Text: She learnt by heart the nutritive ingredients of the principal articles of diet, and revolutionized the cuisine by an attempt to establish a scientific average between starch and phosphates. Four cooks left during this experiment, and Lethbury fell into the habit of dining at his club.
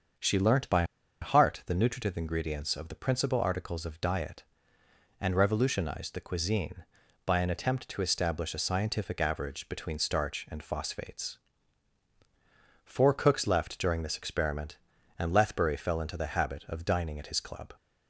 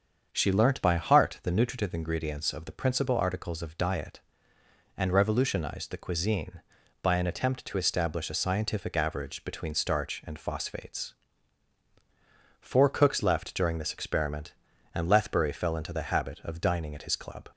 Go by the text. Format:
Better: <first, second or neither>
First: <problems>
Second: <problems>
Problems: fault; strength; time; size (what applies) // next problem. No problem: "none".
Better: second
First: starts louder than the rest; until 1.5 s; 7 dB // pauses between "by" and "heart"; at 0.8 s; 0.37 s long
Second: starts louder than the rest; until 1.3 s; 7 dB